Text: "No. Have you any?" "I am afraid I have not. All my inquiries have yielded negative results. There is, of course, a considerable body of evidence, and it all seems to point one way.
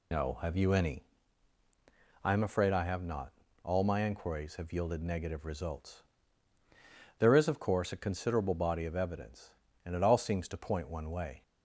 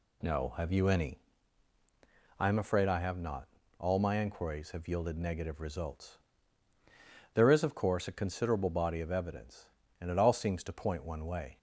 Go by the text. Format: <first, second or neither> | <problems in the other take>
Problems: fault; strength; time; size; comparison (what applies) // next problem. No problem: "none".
second | loses the start of "No"; at 0.1 s; 60 ms